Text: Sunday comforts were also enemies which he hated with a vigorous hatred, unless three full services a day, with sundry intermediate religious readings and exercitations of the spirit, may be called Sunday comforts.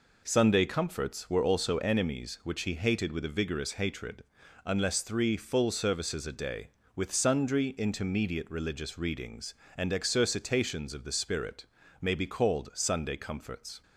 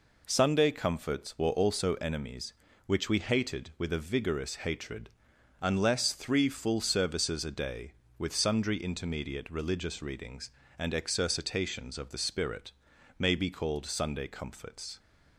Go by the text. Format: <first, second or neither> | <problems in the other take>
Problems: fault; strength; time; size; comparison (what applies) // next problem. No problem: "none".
first | says "we" for "he"; at 3.1 s